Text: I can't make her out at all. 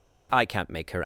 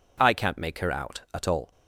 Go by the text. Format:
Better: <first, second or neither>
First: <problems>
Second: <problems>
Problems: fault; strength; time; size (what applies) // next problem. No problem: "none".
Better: second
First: stops before "out at all"; at 1.0 s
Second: none